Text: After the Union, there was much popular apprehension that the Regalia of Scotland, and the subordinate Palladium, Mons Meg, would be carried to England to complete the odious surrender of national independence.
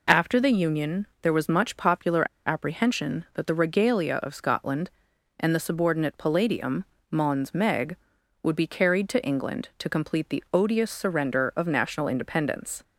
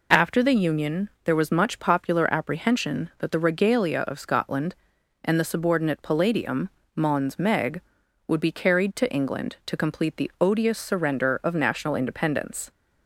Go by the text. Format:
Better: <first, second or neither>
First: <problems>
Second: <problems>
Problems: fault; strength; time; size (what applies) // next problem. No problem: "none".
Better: second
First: pauses between "popular" and "apprehension"; slight; at 2.2 s; 0.20 s long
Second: none